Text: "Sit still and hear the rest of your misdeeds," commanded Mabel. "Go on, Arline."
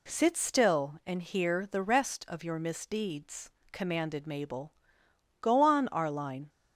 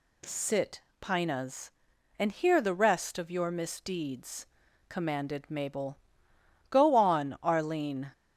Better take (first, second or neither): first